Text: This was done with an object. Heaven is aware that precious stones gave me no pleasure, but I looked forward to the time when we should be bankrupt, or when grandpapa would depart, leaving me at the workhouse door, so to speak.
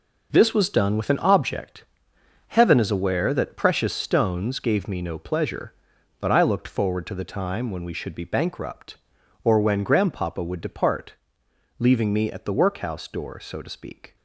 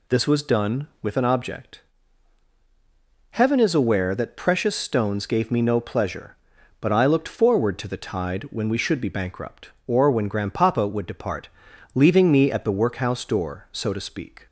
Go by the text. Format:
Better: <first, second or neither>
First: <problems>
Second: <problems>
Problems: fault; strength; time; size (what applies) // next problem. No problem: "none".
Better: first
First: none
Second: says "tide" for "time"; at 7.9 s